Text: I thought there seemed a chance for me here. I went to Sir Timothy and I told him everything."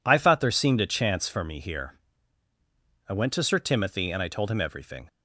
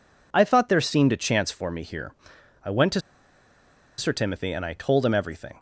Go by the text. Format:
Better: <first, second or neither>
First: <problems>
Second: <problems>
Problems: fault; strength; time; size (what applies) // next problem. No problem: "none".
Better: first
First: none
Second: pauses between "to" and "Sir"; noticeable; at 3.0 s; 0.97 s long